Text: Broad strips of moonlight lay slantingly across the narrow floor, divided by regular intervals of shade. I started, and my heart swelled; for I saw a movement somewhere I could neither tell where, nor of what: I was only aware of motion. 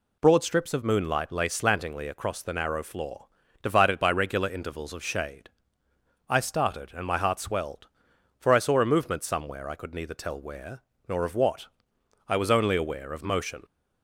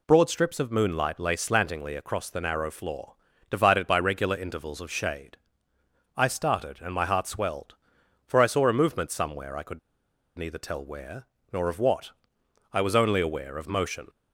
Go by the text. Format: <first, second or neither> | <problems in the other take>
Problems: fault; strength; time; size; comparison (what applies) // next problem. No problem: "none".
first | pauses between "could" and "neither"; noticeable; at 9.7 s; 0.58 s long